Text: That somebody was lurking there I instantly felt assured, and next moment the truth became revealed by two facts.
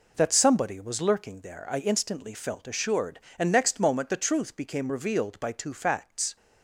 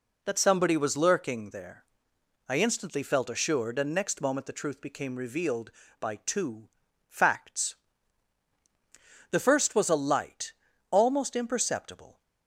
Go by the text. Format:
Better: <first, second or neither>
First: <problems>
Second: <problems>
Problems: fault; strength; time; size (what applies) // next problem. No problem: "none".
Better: first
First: none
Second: pauses between "there" and "I"; noticeable; at 1.8 s; 0.64 s long // pauses between "two" and "facts"; at 6.6 s; 0.40 s long // goes on to say "The first was a light almost imperceptible"; strong; from 9.2 s on; 2.9 s long